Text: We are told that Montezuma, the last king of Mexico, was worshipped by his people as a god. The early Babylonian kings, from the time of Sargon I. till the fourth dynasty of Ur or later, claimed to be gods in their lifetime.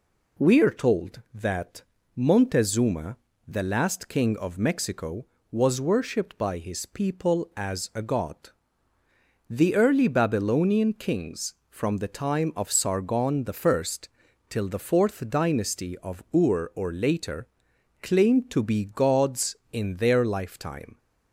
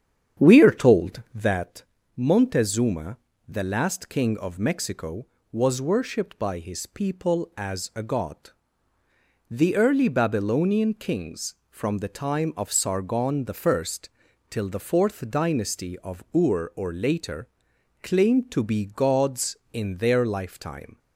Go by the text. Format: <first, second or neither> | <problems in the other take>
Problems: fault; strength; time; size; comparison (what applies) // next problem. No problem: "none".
first | starts louder than the rest; strong; until 1.7 s; 8.5 dB // pauses between "that" and "Montezuma"; slight; at 1.8 s; 0.34 s long; slight in the first // pauses between "I" and "till"; noticeable; at 13.8 s; 0.64 s long; noticeable in the first